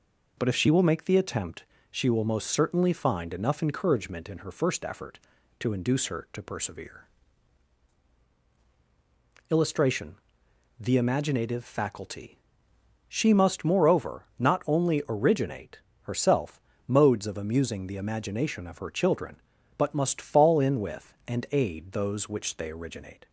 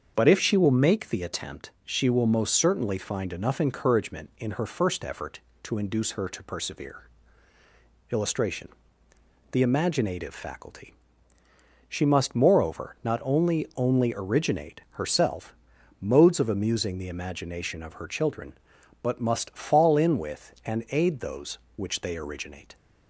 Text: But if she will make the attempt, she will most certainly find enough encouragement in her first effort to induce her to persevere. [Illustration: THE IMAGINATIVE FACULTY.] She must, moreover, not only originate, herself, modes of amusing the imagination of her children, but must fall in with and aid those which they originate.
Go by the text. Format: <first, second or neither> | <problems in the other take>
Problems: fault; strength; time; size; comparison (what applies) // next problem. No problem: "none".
first | starts louder than the rest; until 1.1 s; 7 dB // says "only" twice; at 13.7 s